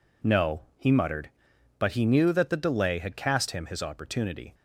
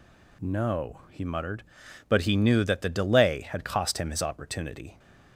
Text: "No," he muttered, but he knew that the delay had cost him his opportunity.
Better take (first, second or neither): second